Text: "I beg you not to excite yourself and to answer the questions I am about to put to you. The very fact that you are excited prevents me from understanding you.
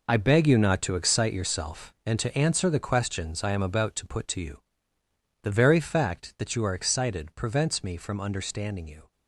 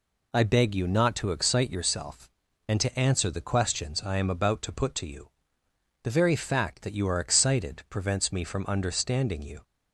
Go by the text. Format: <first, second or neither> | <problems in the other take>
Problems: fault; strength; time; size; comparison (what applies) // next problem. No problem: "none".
second | gets quieter; strong; throughout; 11 dB